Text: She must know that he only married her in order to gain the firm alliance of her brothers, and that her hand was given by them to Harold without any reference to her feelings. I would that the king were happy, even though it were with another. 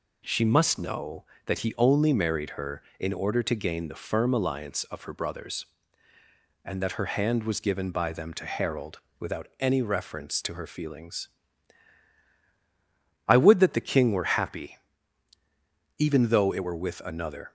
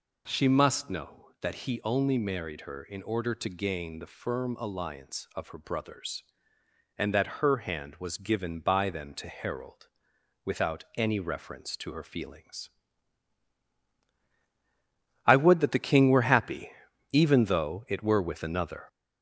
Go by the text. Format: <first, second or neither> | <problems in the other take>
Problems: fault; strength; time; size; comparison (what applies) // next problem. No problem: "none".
first | gets louder; throughout; 4 dB // pauses between "Harold" and "without"; noticeable; at 9.8 s; 0.56 s long; slight in the first